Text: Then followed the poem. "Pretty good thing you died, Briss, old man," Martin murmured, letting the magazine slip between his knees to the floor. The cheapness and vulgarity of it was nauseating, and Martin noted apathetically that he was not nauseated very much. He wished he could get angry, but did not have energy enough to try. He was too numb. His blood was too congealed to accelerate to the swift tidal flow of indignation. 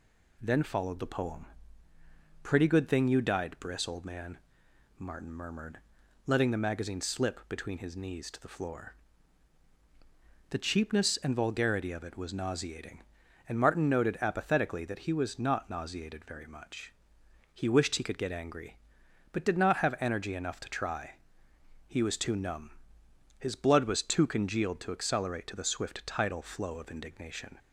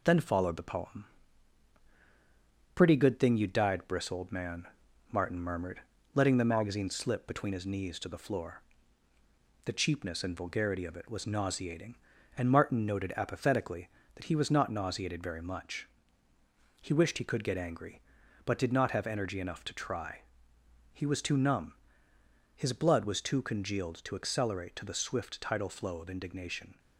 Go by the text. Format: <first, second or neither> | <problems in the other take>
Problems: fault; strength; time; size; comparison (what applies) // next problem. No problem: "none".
first | gets quieter; slight; throughout; 2 dB